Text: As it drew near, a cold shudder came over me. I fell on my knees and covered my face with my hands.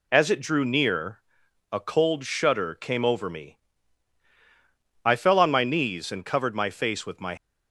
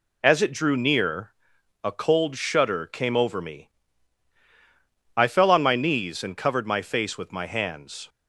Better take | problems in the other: second | stops before "hands"; at 7.3 s

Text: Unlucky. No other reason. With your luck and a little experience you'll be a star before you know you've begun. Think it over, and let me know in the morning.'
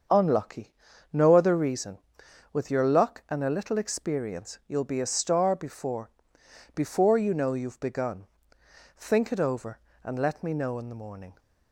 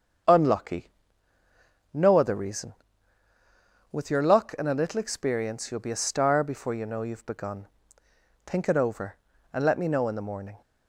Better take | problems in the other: second | starts louder than the rest; until 1.5 s; 7 dB; strong in the second // says "before" twice; at 6.7 s

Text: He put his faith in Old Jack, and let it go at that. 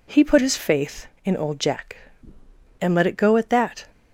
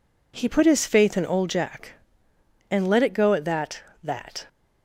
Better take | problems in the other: first | says "that" twice; at 4.0 s

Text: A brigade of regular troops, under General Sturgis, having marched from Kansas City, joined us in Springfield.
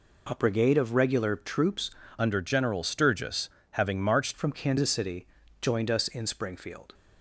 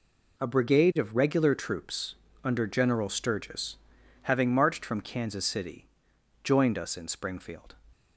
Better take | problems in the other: second | changes voice from "under" to "marched"; from 2.1 to 4.3 s; 2.2 s long

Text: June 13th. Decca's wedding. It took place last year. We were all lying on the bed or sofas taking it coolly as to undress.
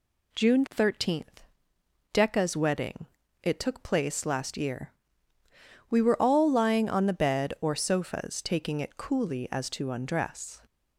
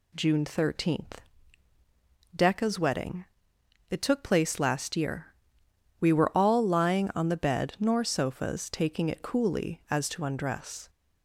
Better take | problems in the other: first | says "nor" for "or"; at 7.7 s

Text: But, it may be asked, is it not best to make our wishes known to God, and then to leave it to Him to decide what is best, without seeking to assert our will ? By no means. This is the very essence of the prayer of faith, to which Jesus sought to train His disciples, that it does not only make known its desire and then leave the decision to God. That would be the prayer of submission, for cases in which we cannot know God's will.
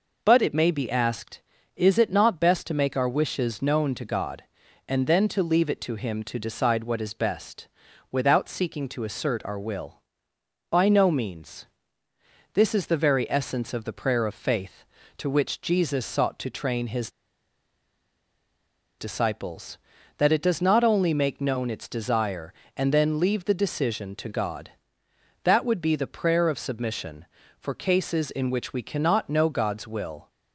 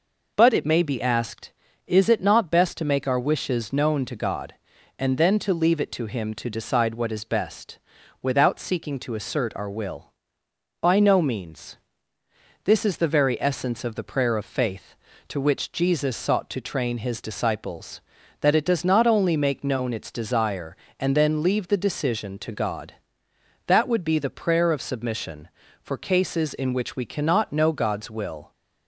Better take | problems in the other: second | pauses between "His" and "disciples"; strong; at 17.0 s; 1.8 s long

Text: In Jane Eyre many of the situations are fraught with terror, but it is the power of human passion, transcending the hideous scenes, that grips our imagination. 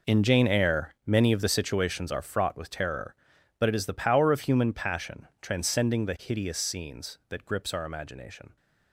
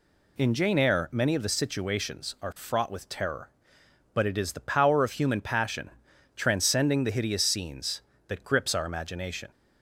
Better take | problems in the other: second | gets quieter; strong; throughout; 14 dB

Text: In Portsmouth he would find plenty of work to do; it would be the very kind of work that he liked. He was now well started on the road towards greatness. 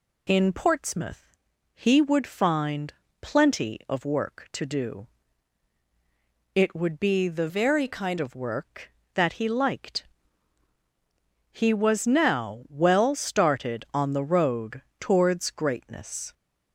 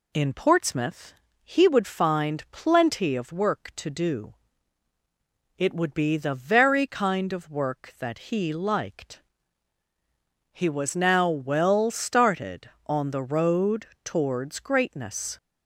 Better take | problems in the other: second | pauses between "Portsmouth" and "he"; slight; at 1.3 s; 0.36 s long; slight in the second // pauses between "find" and "plenty"; slight; at 2.9 s; 0.30 s long // changes voice from "very" to "kind"; from 7.4 to 8.1 s; 0.7 s long // pauses between "road" and "towards"; slight; at 14.8 s; 0.18 s long; slight in the second

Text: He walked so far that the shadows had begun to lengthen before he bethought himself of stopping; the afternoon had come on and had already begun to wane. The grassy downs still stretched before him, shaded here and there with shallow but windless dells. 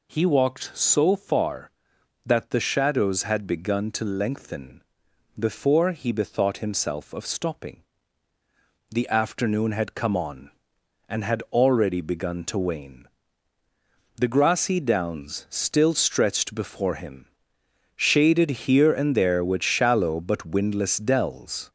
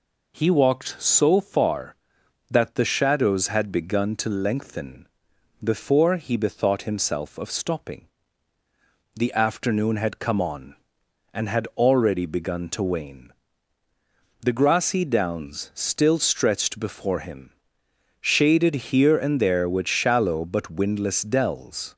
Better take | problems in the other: second | gets louder; throughout; 4 dB // pauses between "lengthen" and "before"; noticeable; at 4.8 s; 0.56 s long; noticeable in the second

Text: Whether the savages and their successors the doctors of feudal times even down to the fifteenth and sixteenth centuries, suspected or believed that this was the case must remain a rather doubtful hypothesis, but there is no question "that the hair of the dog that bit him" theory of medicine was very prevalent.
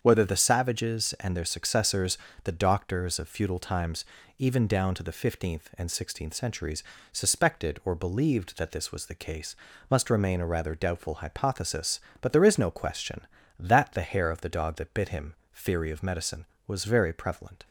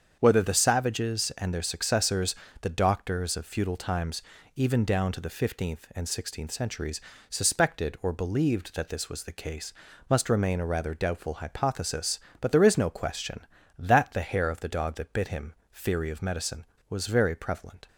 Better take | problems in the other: neither | starts louder than the rest; strong; the same in both // pauses between "successors" and "the"; slight; the same in both // pauses between "times" and "even"; slight; the same in both // pauses between "case" and "must"; the same in both // pauses between "him" and "theory"; slight; the same in both

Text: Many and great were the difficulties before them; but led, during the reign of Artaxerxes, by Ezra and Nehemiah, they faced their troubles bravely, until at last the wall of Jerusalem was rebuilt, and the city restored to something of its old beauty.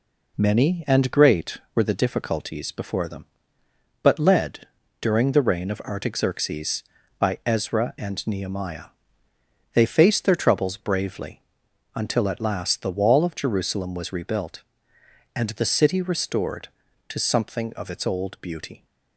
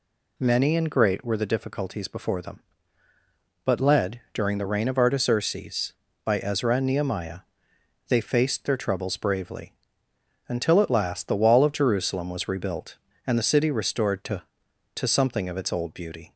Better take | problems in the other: first | says "to" twice; at 14.9 s

